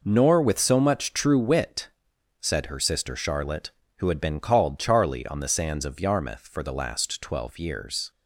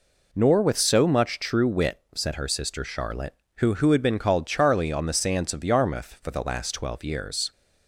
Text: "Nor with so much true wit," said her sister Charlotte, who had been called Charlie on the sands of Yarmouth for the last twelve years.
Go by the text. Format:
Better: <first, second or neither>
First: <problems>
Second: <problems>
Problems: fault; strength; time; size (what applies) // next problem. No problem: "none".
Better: first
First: none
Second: says "who" twice; at 3.7 s